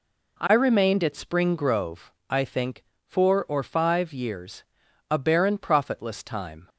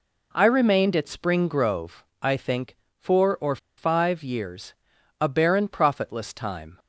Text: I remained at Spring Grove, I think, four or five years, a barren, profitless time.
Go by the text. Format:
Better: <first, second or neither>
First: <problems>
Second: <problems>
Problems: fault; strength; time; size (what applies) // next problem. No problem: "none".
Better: first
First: none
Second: pauses between "or" and "five"; slight; at 3.5 s; 0.20 s long